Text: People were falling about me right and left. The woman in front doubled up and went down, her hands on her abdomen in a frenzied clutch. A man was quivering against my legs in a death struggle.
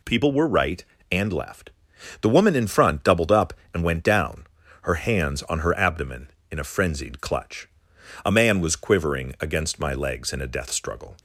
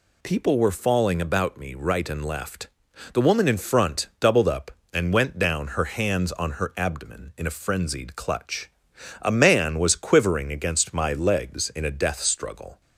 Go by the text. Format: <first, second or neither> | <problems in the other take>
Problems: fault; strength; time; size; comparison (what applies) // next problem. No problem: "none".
second | skips "falling about me"; at 0.4 s